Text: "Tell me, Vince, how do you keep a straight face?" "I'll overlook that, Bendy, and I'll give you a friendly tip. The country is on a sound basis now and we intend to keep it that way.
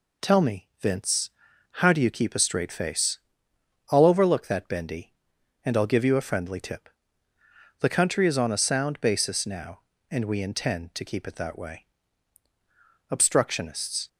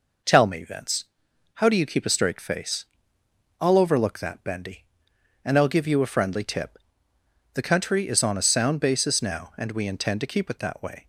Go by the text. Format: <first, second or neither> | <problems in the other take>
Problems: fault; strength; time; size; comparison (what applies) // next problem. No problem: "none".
second | goes on to say "Obstructionists"; noticeable; from 13.0 s on; 0.98 s long